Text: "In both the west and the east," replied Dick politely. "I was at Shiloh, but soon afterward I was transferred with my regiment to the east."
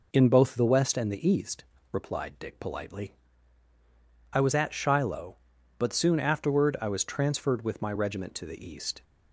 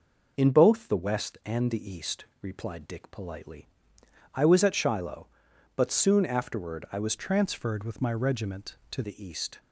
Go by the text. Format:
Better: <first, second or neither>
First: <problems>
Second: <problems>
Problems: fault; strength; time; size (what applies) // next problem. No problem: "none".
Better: first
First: none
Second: changes voice from "transferred" to "to"; from 7.1 to 9.0 s; 1.9 s long